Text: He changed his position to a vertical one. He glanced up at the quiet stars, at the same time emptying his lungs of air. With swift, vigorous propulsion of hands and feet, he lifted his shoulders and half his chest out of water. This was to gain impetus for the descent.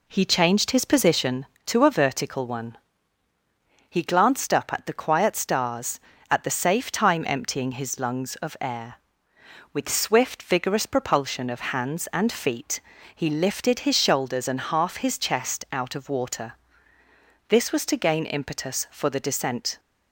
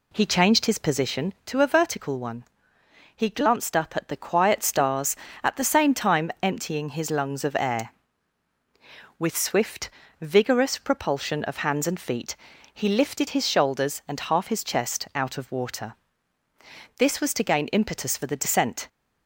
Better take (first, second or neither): second